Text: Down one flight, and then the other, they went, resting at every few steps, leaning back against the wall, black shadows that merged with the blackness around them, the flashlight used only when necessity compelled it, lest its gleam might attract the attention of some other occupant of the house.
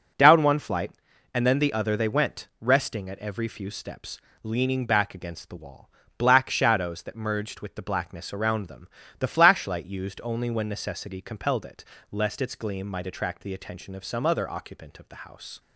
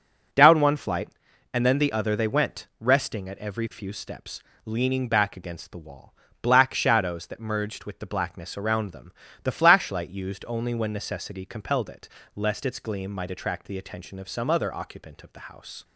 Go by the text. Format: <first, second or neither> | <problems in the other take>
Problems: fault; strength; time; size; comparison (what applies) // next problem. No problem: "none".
neither | none